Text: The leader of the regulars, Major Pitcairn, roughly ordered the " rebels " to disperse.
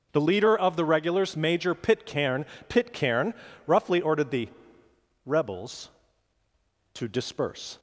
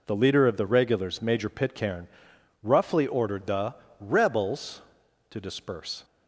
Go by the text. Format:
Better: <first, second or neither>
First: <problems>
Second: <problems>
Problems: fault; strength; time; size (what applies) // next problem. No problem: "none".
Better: second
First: says "Pitcairn" twice; at 2.6 s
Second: none